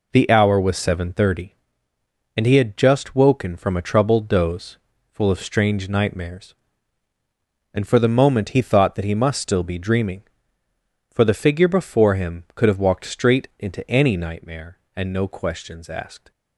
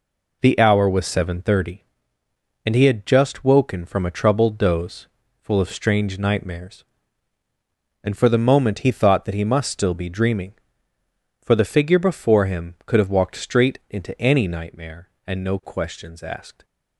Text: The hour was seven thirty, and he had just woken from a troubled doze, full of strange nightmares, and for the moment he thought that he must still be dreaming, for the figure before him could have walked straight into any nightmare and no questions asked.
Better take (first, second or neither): neither